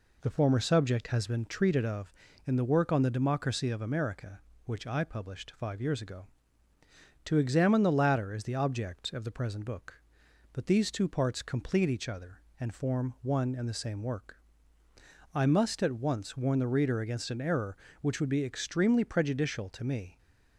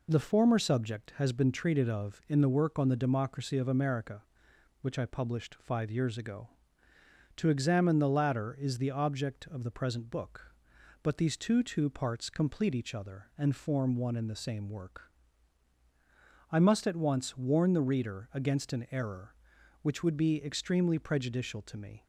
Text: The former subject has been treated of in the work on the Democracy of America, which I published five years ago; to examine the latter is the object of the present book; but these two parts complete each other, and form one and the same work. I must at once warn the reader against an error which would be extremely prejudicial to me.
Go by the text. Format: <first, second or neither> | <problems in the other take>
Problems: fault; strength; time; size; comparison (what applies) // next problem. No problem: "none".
first | says "two" twice; at 11.6 s